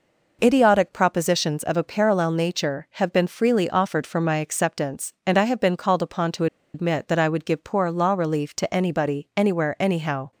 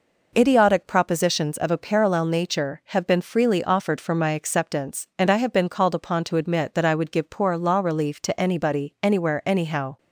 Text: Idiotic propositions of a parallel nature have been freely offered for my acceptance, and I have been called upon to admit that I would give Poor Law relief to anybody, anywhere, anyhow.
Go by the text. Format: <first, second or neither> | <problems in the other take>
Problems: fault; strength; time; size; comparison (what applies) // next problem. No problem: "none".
second | pauses between "to" and "admit"; slight; at 6.4 s; 0.28 s long